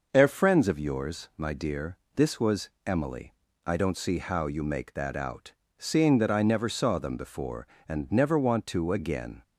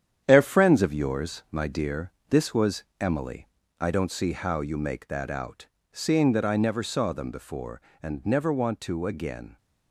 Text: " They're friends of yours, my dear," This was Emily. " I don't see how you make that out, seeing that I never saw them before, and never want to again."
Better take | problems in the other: first | gets quieter; noticeable; throughout; 5.5 dB // pauses between "was" and "Emily"; slight; at 2.8 s; 0.16 s long; slight in the first

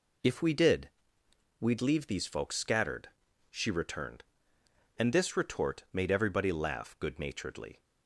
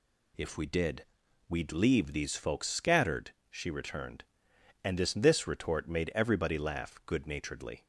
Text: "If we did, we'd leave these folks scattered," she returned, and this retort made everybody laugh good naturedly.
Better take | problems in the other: first | says "this" twice; at 5.1 s

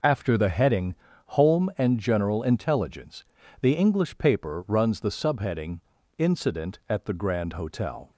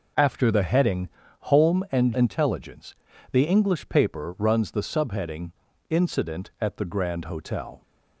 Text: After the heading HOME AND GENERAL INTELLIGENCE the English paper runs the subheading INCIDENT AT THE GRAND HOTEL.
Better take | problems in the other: first | pauses between "heading" and "HOME"; slight; at 1.0 s; 0.32 s long; slight in the first // skips "GENERAL"; at 2.1 s // pauses between "INTELLIGENCE" and "the"; at 2.9 s; 0.38 s long; also in the first // pauses between "subheading" and "INCIDENT"; at 5.5 s; 0.38 s long; also in the first

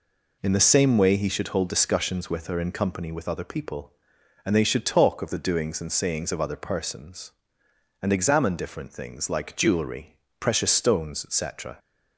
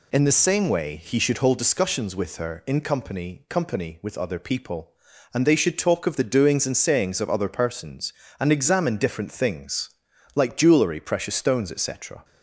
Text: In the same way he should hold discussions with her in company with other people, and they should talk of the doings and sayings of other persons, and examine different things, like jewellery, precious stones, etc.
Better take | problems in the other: first | says "company" twice; at 3.4 s

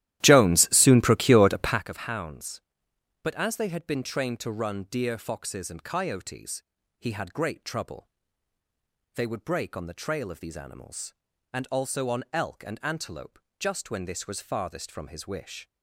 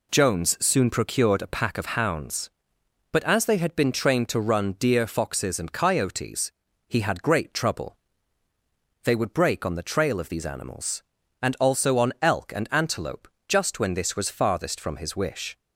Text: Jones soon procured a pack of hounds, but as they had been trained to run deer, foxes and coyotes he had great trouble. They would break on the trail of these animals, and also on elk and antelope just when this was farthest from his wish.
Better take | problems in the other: second | starts louder than the rest; strong; until 1.9 s; 13.5 dB // pauses between "coyotes" and "he"; at 6.6 s; 0.38 s long; also in the second // pauses between "antelope" and "just"; slight; at 13.3 s; 0.18 s long; slight in the second

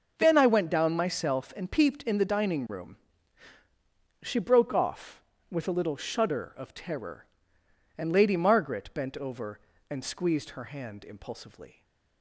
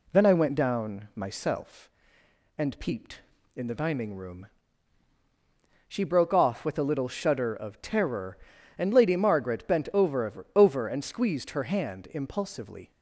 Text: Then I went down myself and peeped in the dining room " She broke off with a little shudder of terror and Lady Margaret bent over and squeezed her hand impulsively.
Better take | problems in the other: first | says "over" twice; at 10.5 s

